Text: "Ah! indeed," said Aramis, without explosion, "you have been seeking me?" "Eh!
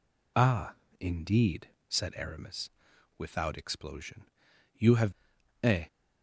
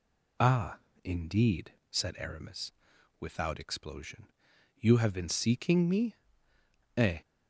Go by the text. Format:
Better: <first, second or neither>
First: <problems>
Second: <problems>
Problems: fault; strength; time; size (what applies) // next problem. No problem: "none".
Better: second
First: skips "been seeking me"; at 5.3 s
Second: none